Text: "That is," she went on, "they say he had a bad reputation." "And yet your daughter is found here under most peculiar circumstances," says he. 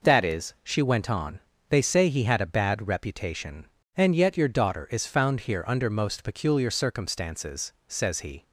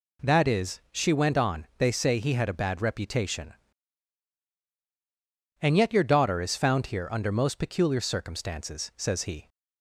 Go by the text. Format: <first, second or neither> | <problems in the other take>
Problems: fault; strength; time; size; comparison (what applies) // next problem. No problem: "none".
neither | none